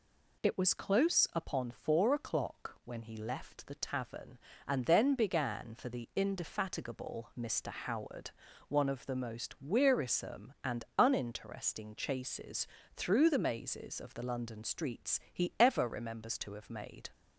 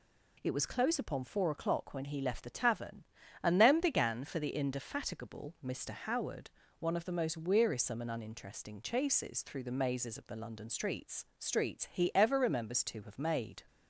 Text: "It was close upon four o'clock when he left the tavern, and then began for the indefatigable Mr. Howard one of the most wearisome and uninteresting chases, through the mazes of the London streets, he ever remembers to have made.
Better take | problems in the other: first | pauses between "Howard" and "one"; slight; at 6.4 s; 0.30 s long; also in the first // says "streets" twice; at 11.4 s

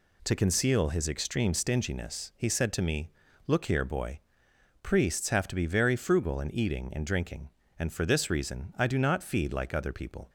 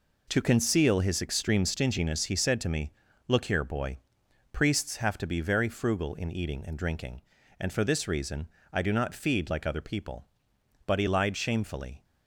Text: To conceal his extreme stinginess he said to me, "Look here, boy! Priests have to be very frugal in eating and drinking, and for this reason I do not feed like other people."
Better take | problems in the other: first | pauses between "reason" and "I"; slight; at 8.4 s; 0.24 s long // goes on to say "But he lied shamefully"; noticeable; from 10.8 s on; 1.1 s long

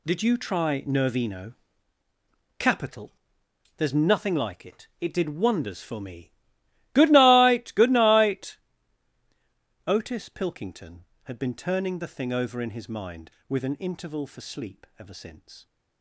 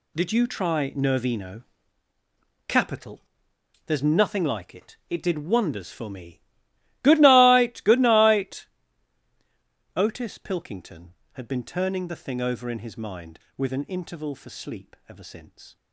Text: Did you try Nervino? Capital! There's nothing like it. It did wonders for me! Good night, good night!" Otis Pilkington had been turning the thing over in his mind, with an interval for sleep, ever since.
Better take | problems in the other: neither | none

